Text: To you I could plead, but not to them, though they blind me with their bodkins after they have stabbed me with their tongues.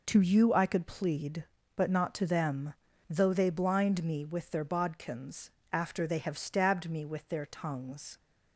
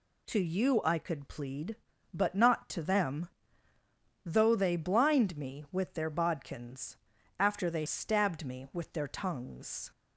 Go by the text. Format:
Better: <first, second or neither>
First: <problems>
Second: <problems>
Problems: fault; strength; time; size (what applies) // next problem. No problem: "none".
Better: first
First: pauses between "bodkins" and "after"; slight; at 5.5 s; 0.20 s long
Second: pauses between "bodkins" and "after"; at 6.9 s; 0.42 s long // skips "have"; at 7.8 s